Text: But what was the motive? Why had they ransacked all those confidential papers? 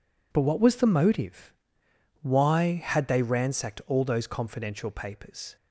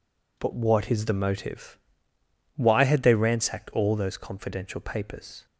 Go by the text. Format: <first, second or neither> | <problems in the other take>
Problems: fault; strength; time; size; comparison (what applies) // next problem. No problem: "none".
first | says "is" for "was"; at 0.9 s